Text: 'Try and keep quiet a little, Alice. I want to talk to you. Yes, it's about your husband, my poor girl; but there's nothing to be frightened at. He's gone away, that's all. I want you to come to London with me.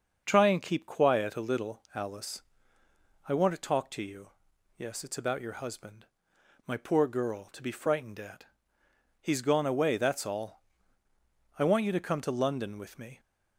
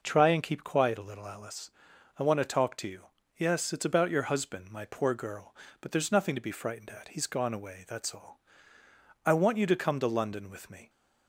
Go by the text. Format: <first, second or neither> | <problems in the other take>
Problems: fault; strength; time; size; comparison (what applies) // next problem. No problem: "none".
second | starts louder than the rest; until 1.2 s; 6.5 dB // skips "but there's nothing"; at 7.4 s